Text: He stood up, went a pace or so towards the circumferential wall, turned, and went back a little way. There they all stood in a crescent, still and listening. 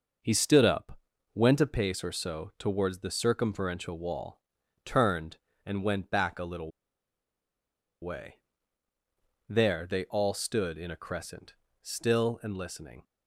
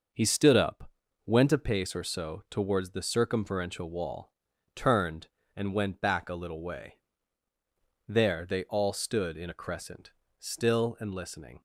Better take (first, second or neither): second